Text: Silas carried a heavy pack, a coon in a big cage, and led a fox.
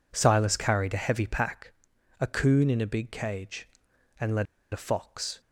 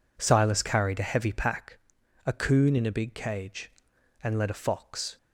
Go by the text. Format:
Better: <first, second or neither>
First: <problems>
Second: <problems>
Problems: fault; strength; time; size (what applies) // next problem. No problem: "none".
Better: second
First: pauses between "led" and "a"; slight; at 4.4 s; 0.26 s long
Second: none